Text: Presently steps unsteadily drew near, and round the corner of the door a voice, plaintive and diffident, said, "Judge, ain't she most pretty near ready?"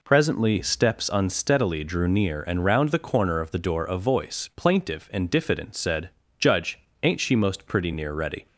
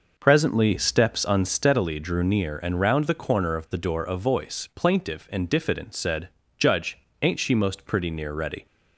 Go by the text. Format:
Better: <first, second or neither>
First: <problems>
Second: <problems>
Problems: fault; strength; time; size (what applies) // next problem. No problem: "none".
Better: first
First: none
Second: starts louder than the rest; noticeable; until 1.9 s; 5.5 dB